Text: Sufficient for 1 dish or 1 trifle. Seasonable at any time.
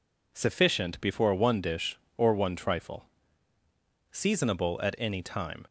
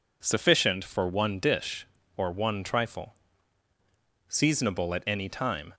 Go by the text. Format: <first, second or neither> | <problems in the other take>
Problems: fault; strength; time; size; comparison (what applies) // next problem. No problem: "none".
second | says "before" for "for"; at 0.9 s